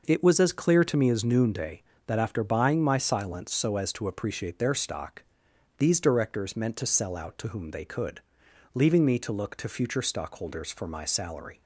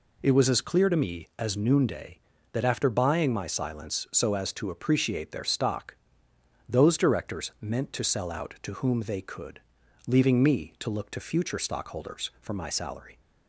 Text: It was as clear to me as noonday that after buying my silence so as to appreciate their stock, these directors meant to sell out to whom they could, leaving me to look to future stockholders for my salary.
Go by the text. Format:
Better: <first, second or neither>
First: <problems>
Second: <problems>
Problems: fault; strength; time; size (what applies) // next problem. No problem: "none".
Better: first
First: none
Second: says "those" for "these"; at 6.6 s